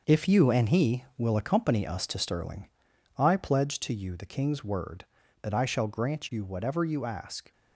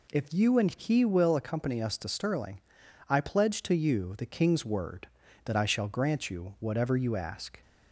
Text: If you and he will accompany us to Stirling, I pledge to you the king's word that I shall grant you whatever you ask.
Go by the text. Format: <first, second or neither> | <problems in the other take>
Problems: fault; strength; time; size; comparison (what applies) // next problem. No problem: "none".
second | gets quieter; strong; throughout; 8 dB